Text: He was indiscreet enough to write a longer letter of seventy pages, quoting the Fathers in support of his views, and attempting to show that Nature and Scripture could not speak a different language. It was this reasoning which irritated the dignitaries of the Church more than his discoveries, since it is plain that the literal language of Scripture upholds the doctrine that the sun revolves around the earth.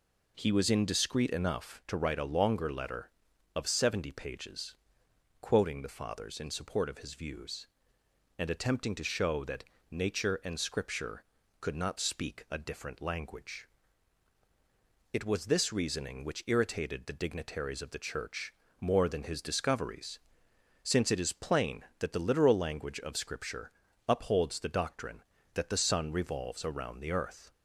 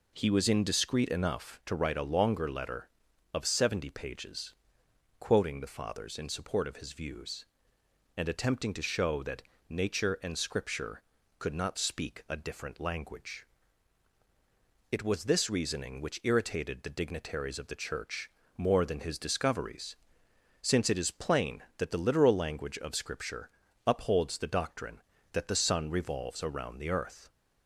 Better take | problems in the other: neither | pauses between "that" and "Nature"; slight; the same in both // pauses between "Church" and "more"; slight; the same in both // pauses between "Scripture" and "upholds"; the same in both

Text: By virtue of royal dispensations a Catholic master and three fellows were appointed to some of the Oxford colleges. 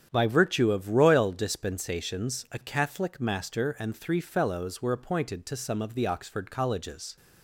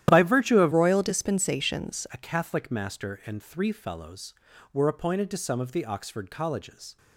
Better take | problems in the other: first | starts louder than the rest; strong; until 1.0 s; 12 dB; strong in the first // changes voice from "royal" to "dispensations"; from 0.7 to 2.0 s; 1.3 s long

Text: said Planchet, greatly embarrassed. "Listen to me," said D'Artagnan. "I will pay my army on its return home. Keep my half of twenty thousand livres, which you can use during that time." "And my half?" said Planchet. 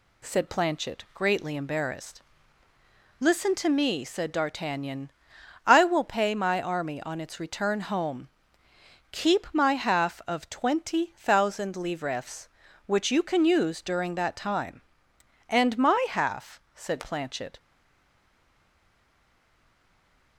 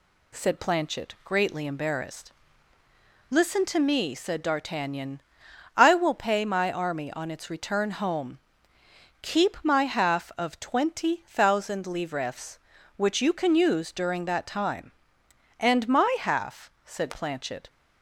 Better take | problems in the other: second | stays silent after the last word; strong; from 17.5 s on; 2.8 s long

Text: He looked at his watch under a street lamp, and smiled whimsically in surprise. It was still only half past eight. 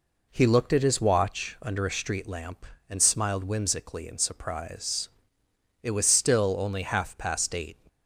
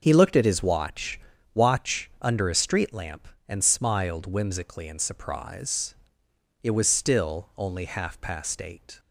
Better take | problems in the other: first | starts louder than the rest; until 1.0 s; 6.5 dB // says "watch" twice; at 1.5 s

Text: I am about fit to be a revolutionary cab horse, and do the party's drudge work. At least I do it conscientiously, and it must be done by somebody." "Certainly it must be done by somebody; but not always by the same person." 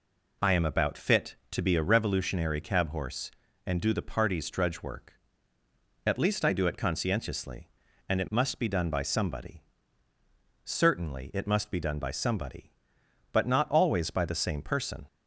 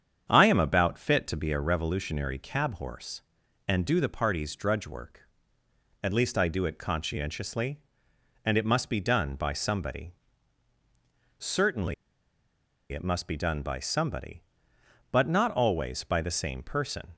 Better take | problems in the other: first | starts louder than the rest; strong; until 1.3 s; 8 dB // pauses between "Certainly" and "it"; noticeable; at 11.9 s; 0.97 s long

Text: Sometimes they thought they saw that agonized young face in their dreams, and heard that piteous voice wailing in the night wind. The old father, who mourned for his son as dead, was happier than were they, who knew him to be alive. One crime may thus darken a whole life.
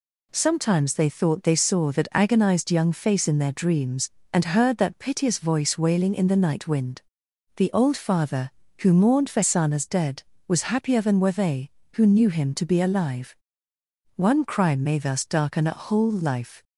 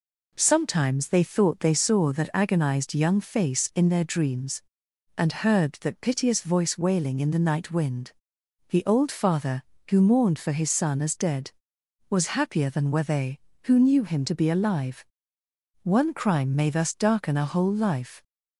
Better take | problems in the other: second | skips "his"; at 9.4 s

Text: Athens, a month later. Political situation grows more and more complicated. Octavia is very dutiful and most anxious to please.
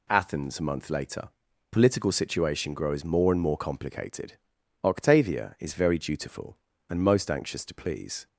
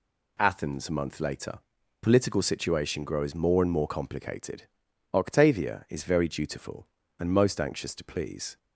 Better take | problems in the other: neither | none

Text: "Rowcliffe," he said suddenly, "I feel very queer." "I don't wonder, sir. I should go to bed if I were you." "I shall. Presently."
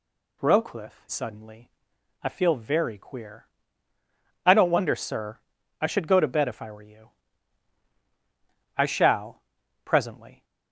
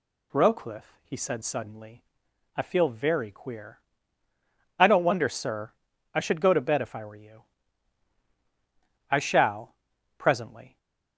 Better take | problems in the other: second | skips "he said"; at 1.0 s

